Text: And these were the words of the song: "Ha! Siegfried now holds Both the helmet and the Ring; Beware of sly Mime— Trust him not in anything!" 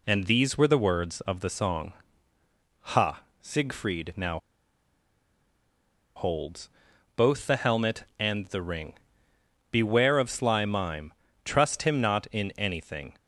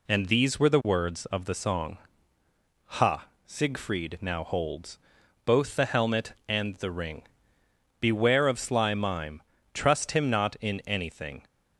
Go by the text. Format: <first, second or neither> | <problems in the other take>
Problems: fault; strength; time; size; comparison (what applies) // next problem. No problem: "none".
second | pauses between "now" and "holds"; strong; at 4.3 s; 1.7 s long // pauses between "holds" and "Both"; noticeable; at 6.6 s; 0.48 s long; noticeable in the second